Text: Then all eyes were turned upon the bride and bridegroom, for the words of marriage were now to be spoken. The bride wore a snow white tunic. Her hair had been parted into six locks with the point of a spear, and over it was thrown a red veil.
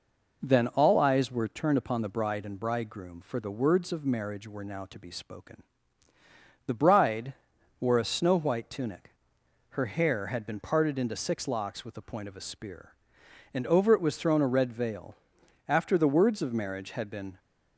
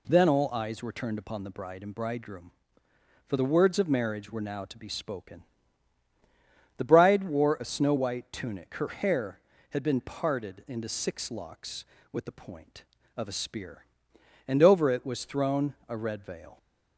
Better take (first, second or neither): second